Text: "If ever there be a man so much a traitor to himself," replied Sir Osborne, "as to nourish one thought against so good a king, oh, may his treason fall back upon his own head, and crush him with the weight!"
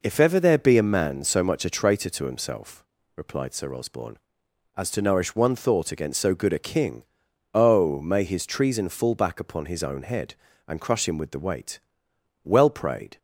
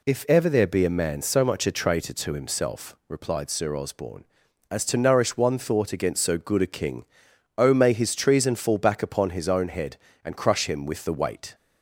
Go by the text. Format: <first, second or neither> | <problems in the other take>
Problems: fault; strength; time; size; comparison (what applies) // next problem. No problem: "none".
second | goes on to say "Well prayed"; noticeable; from 12.4 s on; 0.74 s long